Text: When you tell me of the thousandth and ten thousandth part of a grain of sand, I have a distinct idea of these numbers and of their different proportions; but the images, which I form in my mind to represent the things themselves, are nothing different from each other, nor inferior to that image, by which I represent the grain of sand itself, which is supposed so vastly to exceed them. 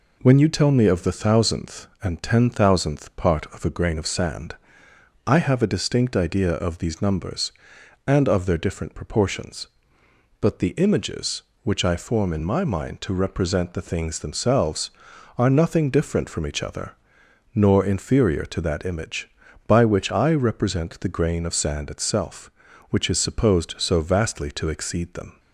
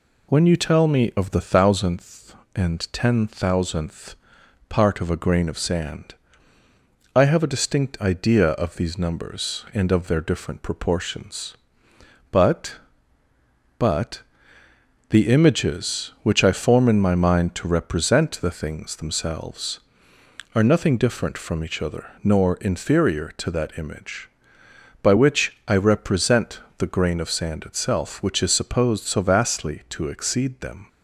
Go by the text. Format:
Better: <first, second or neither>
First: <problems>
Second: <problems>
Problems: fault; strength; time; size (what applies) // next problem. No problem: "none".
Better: first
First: none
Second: pauses between "thousandth" and "part"; noticeable; at 4.1 s; 0.57 s long // says "but" twice; at 13.7 s // pauses between "represent" and "the"; slight; at 26.5 s; 0.18 s long